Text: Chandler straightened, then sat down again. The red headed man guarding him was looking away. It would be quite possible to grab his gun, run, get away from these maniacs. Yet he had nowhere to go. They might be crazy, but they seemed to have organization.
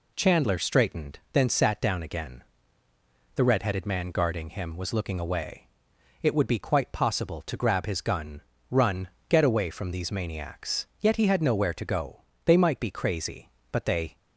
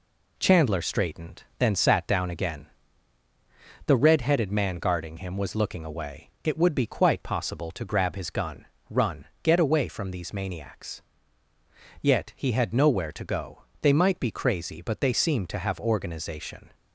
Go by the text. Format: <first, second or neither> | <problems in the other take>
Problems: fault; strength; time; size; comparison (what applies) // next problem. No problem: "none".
second | stops before "seemed to have organization"; at 14.1 s